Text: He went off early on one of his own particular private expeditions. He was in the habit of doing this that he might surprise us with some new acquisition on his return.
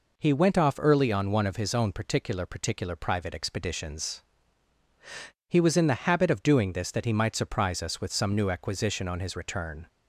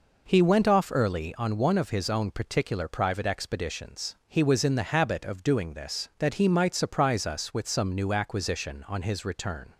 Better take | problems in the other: second | says "particular" twice; at 2.4 s

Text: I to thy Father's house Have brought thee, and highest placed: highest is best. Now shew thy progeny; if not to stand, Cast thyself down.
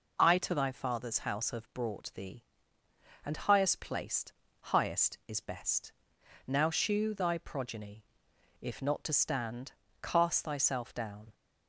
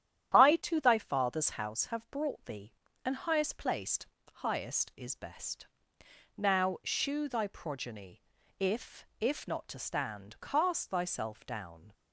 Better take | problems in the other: first | starts louder than the rest; strong; until 1.4 s; 10.5 dB // says "if" twice; at 9.2 s

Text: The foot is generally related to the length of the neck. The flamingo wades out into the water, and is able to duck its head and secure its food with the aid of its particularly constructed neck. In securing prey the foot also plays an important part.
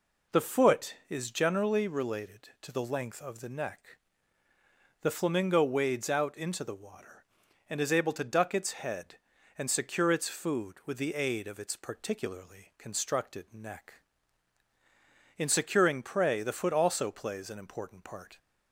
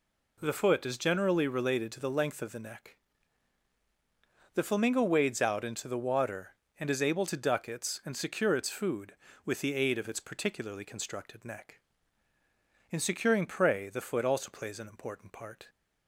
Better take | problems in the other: first | skips "head"; at 8.0 s

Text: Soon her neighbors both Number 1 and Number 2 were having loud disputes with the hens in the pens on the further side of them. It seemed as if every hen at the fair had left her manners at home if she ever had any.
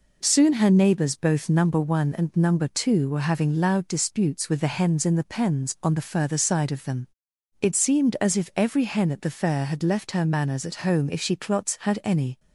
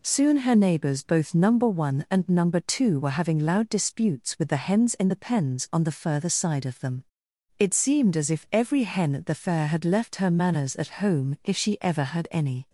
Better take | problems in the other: second | says "clots" for "ever"; at 11.3 s

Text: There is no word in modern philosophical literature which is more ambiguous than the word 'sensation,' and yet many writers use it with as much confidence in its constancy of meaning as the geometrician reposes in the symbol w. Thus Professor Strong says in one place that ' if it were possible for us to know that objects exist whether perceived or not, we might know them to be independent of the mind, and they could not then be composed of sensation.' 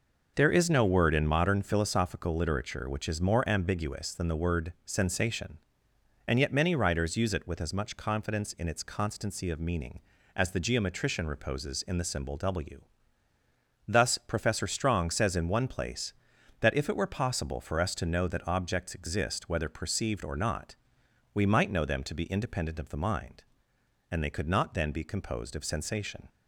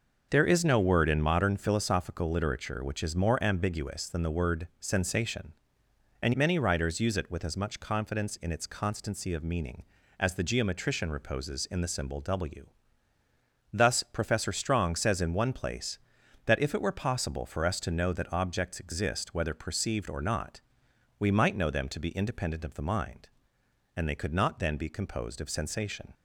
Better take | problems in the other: first | skips "yet"; at 6.3 s

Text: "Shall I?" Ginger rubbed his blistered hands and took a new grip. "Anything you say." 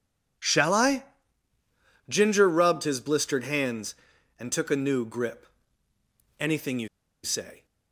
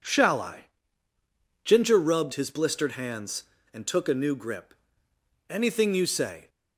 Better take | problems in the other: second | pauses between "you" and "say"; at 6.8 s; 0.36 s long

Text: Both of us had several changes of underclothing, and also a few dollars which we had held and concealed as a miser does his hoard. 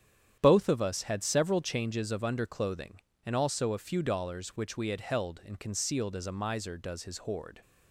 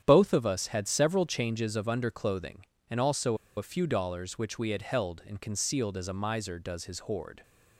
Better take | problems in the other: first | starts louder than the rest; strong; until 1.0 s; 9.5 dB; strong in the first // pauses between "also" and "a"; slight; at 3.3 s; 0.20 s long

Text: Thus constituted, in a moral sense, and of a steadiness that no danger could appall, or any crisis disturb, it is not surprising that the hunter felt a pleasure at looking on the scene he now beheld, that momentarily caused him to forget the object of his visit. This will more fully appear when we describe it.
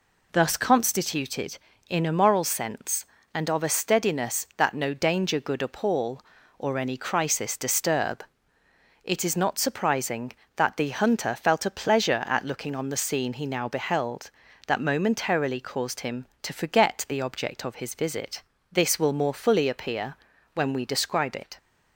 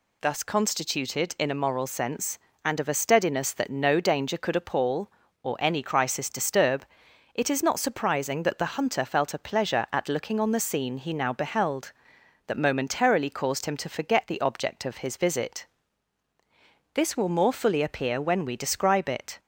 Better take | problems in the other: second | says "good" for "could"; at 5.3 s // pauses between "appear" and "when"; at 20.1 s; 0.38 s long

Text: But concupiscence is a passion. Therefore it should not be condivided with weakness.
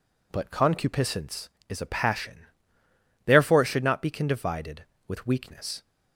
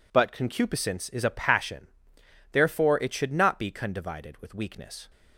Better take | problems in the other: neither | none

